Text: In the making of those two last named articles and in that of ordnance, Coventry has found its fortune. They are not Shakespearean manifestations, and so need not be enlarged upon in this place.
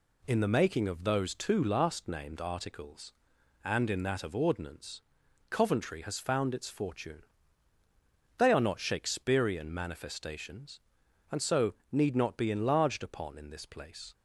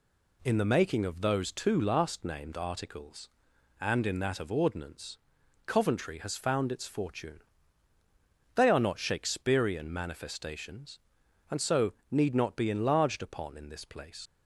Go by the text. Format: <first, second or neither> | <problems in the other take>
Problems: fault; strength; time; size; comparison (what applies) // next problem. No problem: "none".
first | pauses between "so" and "need"; slight; at 11.9 s; 0.18 s long; slight in the first // leaves "place" unfinished; at 14.2 s; 60 ms